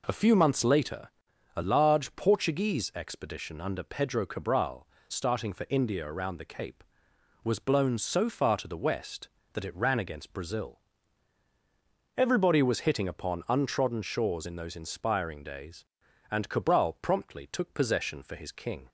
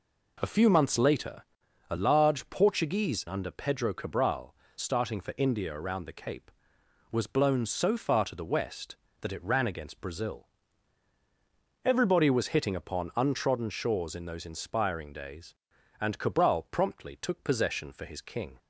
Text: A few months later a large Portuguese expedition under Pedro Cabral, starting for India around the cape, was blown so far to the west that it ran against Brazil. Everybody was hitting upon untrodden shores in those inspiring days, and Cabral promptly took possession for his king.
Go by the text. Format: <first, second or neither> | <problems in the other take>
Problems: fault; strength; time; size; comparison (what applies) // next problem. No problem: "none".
first | pauses between "later" and "a"; noticeable; at 1.4 s; 0.48 s long; noticeable in the first // skips "expedition"; at 3.2 s